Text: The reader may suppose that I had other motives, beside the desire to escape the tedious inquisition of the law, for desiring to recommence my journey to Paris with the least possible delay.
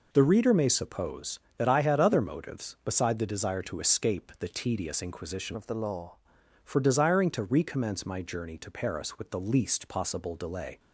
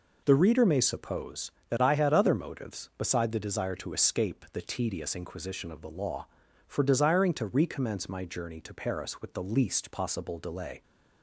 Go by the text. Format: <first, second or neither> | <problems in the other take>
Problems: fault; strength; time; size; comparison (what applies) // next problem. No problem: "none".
second | changes voice from "of" to "law"; from 5.5 to 6.1 s; 0.6 s long